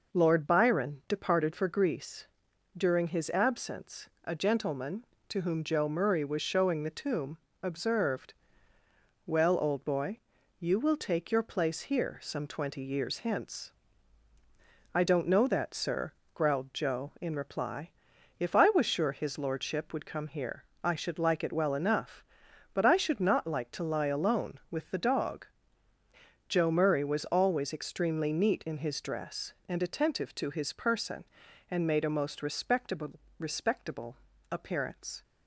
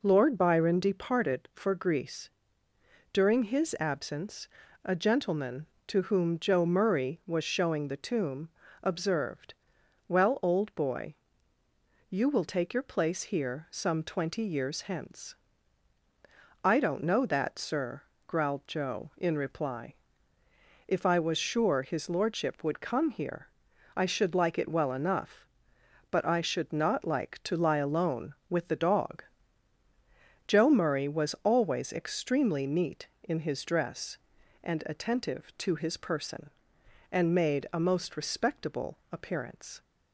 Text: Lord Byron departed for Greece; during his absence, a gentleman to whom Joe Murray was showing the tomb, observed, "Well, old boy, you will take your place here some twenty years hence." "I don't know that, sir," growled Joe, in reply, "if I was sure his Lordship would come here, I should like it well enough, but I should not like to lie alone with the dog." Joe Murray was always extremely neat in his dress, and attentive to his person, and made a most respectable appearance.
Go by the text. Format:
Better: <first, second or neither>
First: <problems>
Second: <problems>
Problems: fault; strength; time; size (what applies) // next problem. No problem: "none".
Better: second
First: says "respectable" twice; at 33.3 s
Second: none